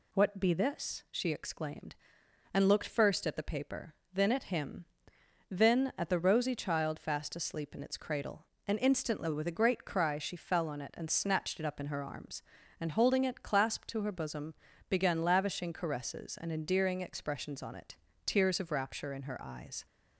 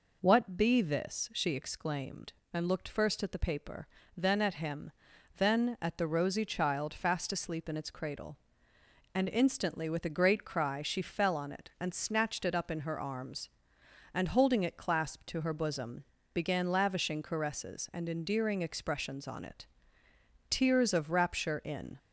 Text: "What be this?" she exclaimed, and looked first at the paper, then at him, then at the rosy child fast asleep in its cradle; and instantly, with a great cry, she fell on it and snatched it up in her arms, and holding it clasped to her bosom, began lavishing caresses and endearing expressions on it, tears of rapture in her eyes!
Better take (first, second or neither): first